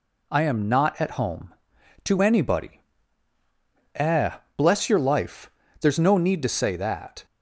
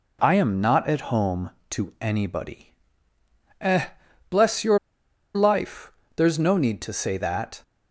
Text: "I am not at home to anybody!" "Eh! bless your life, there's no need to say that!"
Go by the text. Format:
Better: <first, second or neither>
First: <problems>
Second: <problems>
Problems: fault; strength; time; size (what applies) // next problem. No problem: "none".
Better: first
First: none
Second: pauses between "your" and "life"; noticeable; at 4.7 s; 0.56 s long